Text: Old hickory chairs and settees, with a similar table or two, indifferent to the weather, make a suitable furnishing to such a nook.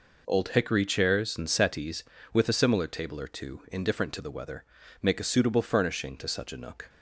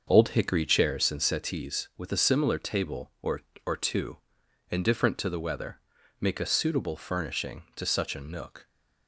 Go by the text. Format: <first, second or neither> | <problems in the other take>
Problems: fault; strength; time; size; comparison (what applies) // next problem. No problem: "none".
first | starts louder than the rest; until 1.0 s; 6.5 dB // says "or" twice; at 3.6 s